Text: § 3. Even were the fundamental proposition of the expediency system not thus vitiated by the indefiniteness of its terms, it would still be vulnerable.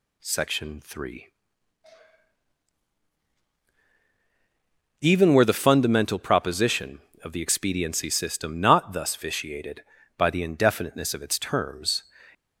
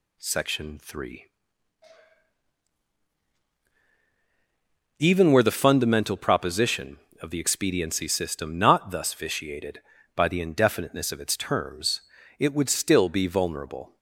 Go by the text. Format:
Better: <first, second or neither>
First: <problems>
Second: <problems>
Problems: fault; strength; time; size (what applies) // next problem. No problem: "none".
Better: second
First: stops before "it would still be vulnerable"; at 12.3 s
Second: none